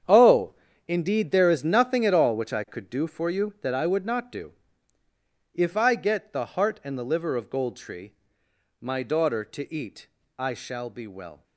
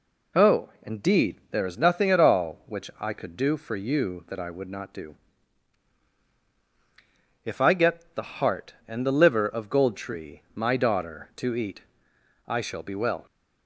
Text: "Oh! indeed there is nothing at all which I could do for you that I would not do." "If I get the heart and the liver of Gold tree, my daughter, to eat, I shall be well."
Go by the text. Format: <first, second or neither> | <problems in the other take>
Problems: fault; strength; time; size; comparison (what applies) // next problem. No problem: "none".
second | gets quieter; strong; throughout; 12.5 dB